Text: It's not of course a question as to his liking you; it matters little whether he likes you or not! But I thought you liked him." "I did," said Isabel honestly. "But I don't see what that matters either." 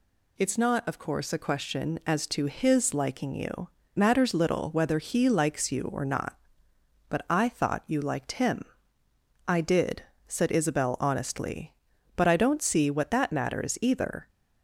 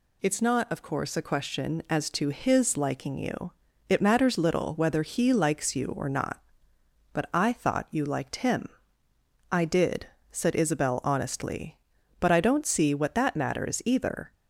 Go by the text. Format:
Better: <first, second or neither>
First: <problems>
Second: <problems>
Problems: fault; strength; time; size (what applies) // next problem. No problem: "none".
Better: second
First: skips "it"; at 3.8 s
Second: none